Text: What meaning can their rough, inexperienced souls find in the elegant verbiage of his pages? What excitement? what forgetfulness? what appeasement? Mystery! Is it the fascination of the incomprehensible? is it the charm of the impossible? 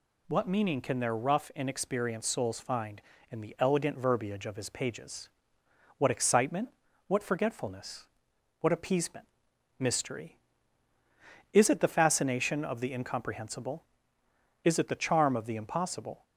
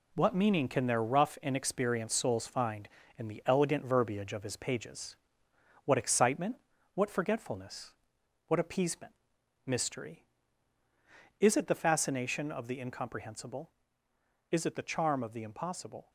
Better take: first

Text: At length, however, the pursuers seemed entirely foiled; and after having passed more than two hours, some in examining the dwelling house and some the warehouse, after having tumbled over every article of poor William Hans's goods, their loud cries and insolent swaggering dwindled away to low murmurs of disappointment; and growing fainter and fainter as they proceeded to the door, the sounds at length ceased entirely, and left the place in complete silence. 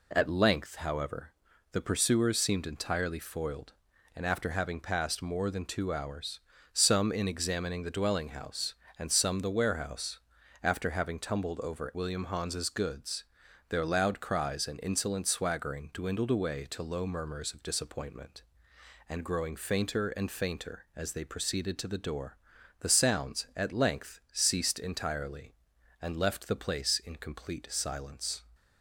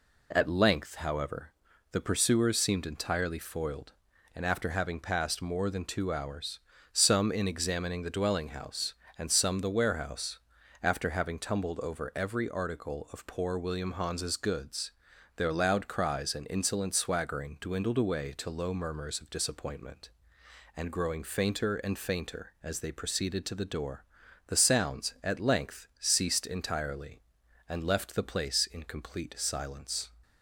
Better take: second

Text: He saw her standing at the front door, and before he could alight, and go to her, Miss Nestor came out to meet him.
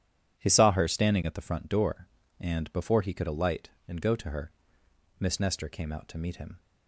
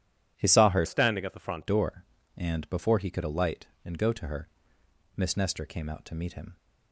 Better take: first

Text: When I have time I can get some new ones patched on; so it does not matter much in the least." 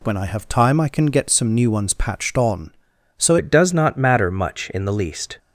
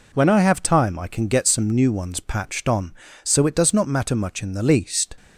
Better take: second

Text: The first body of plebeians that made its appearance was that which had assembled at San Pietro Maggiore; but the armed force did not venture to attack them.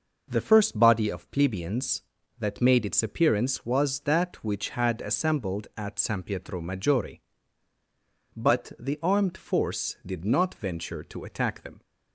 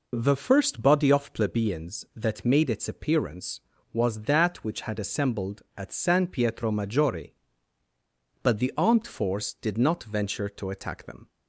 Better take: neither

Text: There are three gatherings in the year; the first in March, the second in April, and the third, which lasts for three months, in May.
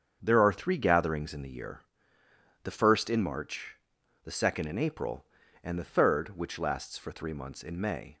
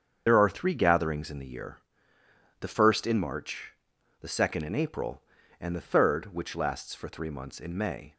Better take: first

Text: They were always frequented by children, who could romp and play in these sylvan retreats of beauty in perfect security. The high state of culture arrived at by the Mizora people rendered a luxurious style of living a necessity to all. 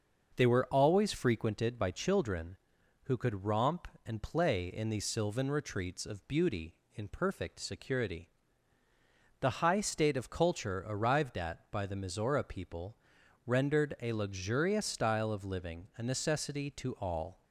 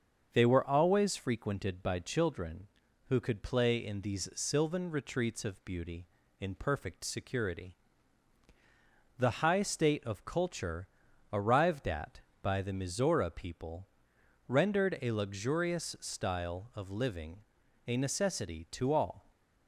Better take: first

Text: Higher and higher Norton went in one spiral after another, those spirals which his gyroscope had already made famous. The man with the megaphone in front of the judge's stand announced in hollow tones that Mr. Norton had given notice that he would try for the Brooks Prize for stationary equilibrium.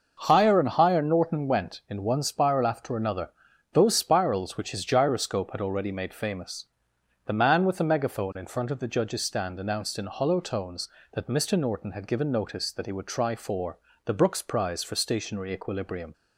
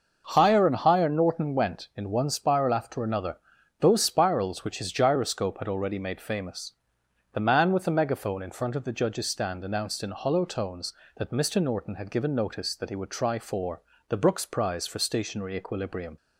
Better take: neither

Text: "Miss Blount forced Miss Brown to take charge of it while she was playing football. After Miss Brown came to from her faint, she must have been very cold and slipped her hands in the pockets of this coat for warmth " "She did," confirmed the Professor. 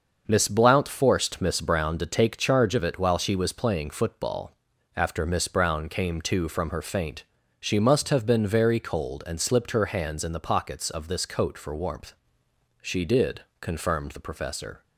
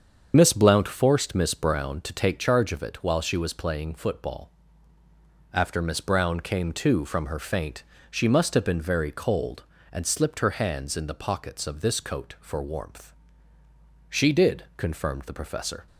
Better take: first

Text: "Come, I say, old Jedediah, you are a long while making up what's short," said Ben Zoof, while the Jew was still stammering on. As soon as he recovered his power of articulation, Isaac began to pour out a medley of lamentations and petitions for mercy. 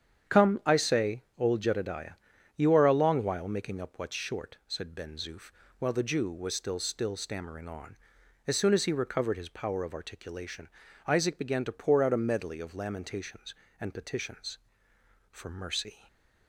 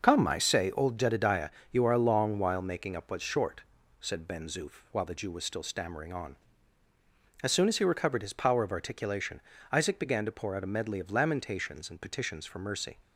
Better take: second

